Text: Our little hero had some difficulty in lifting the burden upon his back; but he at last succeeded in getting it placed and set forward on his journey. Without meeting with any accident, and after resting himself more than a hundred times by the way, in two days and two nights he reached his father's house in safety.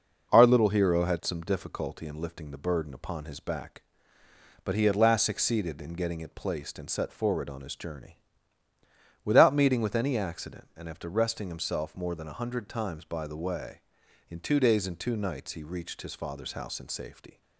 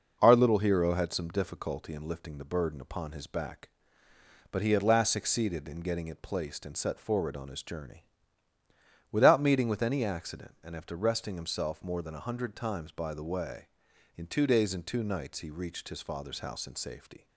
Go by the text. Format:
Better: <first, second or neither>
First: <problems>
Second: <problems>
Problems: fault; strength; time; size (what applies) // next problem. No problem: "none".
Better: neither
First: none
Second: none